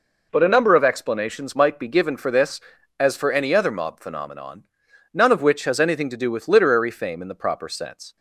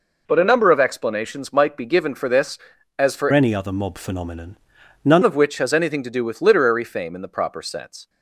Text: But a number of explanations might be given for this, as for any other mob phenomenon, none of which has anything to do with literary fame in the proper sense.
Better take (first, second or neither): first